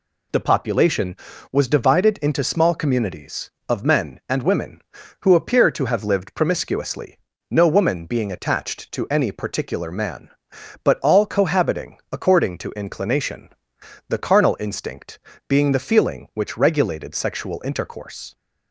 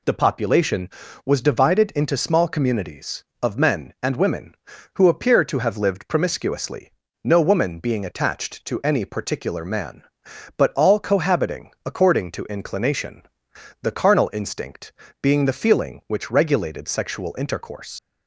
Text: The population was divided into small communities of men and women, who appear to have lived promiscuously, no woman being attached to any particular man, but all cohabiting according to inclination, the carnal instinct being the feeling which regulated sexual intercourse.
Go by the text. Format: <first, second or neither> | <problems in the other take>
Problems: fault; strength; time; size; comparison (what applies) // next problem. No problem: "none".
first | pauses between "instinct" and "being"; slight; at 14.9 s; 0.30 s long; slight in the first // leaves "intercourse" unfinished; at 17.9 s; 100 ms